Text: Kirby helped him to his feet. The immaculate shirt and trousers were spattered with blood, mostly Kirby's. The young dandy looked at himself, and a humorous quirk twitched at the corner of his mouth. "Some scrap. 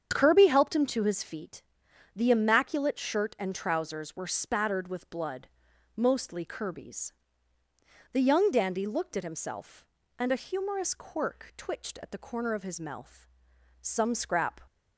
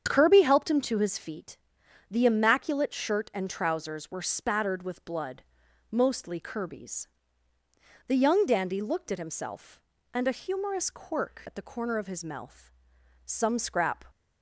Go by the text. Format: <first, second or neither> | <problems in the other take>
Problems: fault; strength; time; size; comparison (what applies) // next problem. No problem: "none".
first | starts louder than the rest; strong; until 1.0 s; 7.5 dB; strong in the first // skips "twitched"; at 11.4 s